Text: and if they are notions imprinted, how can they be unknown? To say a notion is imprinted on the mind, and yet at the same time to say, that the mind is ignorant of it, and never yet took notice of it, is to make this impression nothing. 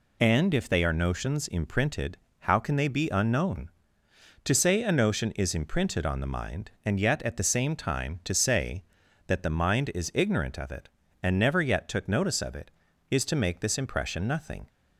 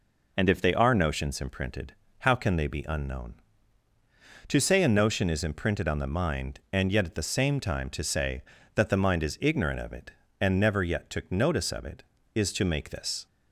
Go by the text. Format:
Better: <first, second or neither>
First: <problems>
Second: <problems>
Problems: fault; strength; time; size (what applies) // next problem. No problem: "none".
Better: first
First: none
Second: stops before "impression nothing"; at 13.2 s